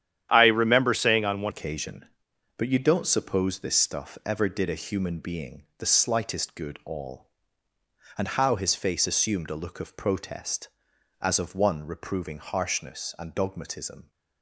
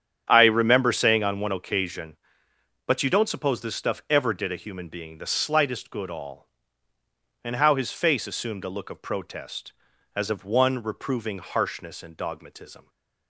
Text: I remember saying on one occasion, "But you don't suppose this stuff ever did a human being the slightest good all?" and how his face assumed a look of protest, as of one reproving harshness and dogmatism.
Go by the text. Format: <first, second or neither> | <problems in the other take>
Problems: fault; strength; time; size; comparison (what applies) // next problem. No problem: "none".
second | starts louder than the rest; strong; until 1.3 s; 10.5 dB; strong in the second // changes voice at "occasion"; from 1.4 s on; 12.7 s long